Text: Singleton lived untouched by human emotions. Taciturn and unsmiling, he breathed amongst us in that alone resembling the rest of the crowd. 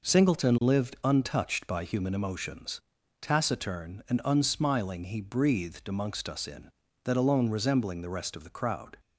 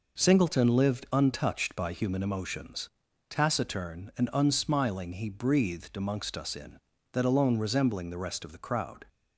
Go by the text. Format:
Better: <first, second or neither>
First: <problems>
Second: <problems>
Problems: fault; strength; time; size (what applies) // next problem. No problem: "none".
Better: neither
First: none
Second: none